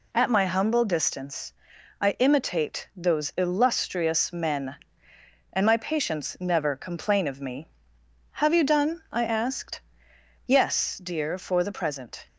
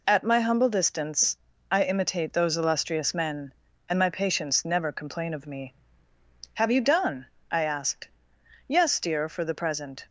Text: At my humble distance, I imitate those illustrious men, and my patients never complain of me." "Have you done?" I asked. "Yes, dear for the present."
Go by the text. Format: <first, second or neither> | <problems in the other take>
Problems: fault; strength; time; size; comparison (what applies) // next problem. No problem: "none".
neither | none